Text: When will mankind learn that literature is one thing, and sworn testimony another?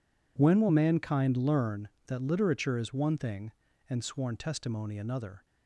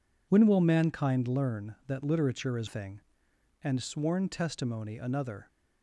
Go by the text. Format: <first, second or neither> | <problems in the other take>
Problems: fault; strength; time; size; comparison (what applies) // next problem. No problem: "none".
first | skips "one"; at 2.6 s